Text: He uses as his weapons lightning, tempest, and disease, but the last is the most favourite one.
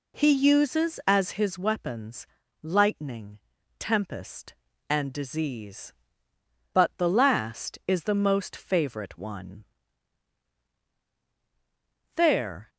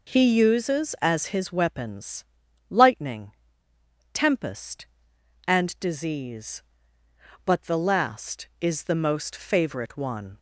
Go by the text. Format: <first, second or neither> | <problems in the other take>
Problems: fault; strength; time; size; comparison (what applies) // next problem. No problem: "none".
second | pauses between "weapons" and "lightning"; at 2.2 s; 0.38 s long; noticeable in the second // goes on to say "There"; from 12.1 s on; 0.54 s long